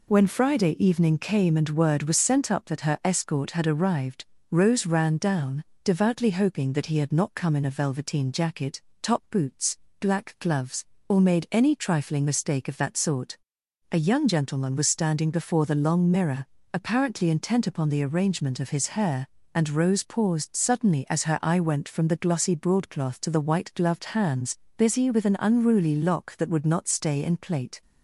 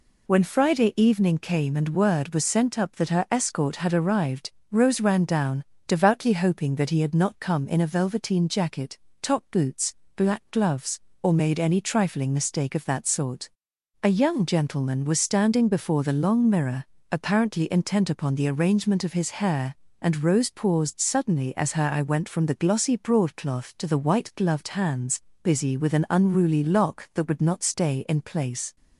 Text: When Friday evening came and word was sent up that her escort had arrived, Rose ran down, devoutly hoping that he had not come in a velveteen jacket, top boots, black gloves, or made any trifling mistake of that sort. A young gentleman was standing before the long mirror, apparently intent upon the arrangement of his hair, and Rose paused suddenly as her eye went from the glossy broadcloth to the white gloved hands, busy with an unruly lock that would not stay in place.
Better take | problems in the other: second | says "plate" for "place"; at 27.3 s

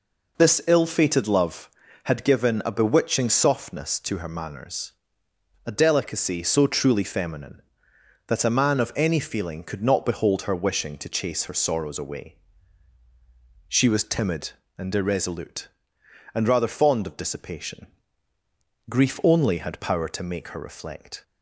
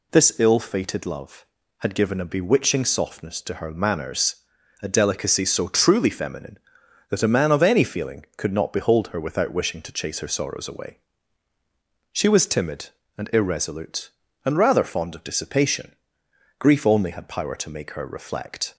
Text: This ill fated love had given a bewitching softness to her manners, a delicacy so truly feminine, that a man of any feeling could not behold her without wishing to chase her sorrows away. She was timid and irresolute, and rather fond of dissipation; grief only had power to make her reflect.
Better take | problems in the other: second | skips "without"; at 10.5 s

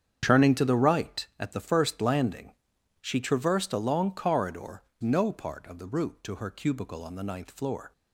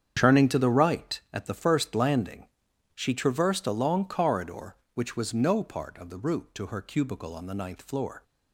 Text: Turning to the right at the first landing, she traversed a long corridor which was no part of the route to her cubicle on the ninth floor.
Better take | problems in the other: second | starts louder than the rest; strong; until 1.2 s; 8 dB; strong in the second // skips "which was"; at 4.9 s

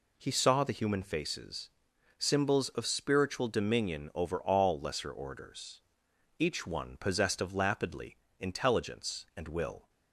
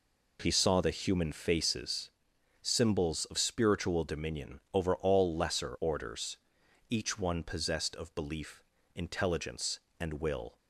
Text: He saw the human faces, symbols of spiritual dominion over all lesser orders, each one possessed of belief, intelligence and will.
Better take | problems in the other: second | says "lapidly" for "belief"; at 7.5 s

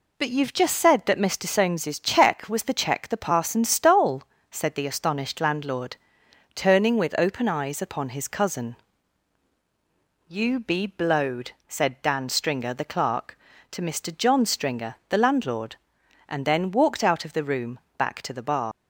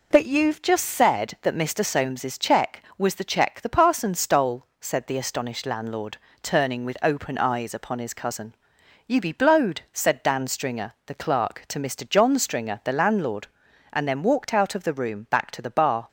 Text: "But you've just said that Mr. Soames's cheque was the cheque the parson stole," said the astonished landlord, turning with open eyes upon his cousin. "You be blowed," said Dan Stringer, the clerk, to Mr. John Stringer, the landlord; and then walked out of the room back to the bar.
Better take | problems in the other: second | pauses between "room" and "back"; slight; at 17.8 s; 0.16 s long // leaves "bar" unfinished; at 18.7 s; 110 ms

